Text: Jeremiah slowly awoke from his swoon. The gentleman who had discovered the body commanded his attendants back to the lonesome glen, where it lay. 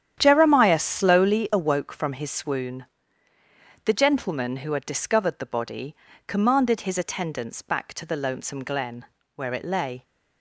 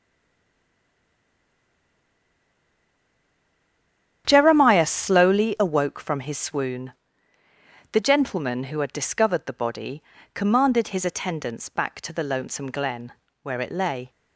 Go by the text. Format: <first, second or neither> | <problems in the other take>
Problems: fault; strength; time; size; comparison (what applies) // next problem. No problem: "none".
first | stays silent before the first word; strong; until 4.2 s; 4.2 s long // starts louder than the rest; strong; until 5.2 s; 9.5 dB; strong in the first // pauses between "body" and "commanded"; slight; at 10.0 s; 0.32 s long; slight in the first